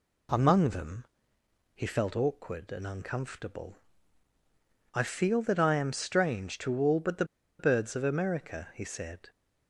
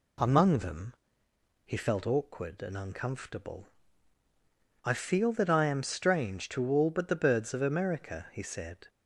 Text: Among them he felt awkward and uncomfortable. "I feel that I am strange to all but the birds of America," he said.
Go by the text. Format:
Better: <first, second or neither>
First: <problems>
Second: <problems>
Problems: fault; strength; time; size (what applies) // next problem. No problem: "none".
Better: second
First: pauses between "them" and "he"; noticeable; at 1.0 s; 0.70 s long // pauses between "the" and "birds"; slight; at 7.2 s; 0.35 s long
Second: pauses between "them" and "he"; noticeable; at 0.9 s; 0.71 s long